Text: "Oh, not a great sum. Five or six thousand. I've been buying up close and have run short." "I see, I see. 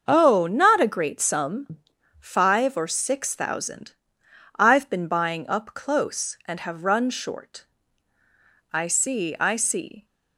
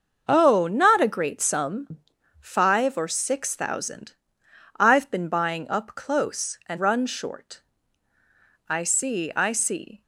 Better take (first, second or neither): first